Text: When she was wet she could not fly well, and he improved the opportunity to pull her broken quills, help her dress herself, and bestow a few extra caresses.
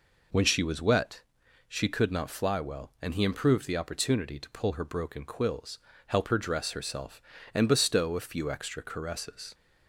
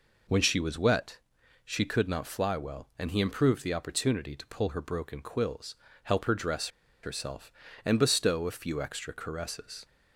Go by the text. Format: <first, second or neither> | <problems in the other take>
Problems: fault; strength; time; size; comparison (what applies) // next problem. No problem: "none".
first | pauses between "wet" and "she"; noticeable; at 1.1 s; 0.46 s long; noticeable in the first // pauses between "dress" and "herself"; slight; at 6.6 s; 0.35 s long